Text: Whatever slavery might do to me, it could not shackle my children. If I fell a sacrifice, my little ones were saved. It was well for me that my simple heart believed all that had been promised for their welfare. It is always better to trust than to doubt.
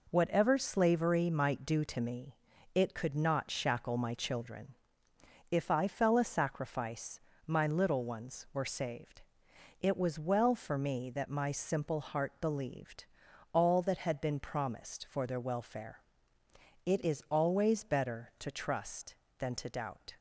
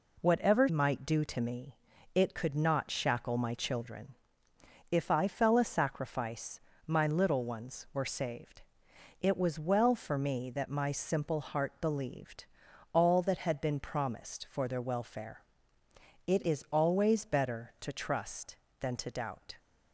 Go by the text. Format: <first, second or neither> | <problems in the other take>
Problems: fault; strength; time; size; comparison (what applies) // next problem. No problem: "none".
first | skips "slavery"; at 0.6 s // pauses between "believed" and "all"; noticeable; at 12.4 s; 0.48 s long; noticeable in the first